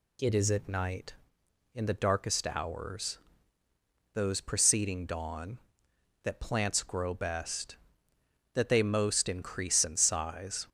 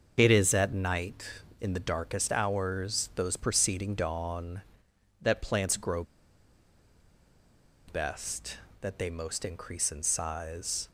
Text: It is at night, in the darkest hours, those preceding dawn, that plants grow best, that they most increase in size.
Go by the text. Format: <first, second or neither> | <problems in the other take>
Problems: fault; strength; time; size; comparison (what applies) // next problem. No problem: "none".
first | starts louder than the rest; noticeable; until 1.1 s; 6 dB // pauses between "grow" and "best"; strong; at 6.0 s; 1.8 s long